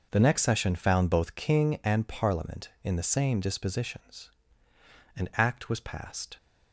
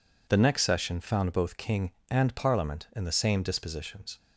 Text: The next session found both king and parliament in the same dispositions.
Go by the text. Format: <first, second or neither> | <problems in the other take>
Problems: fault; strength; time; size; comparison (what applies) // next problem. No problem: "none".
second | goes on to say "An act was passed"; noticeable; from 5.1 s on; 1.2 s long